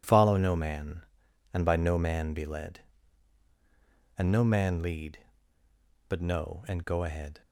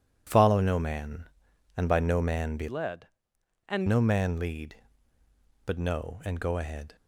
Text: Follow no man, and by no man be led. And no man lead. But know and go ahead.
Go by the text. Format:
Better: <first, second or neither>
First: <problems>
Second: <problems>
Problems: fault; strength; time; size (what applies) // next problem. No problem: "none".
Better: first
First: none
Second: changes voice from "led" to "And"; from 2.6 to 3.8 s; 1.2 s long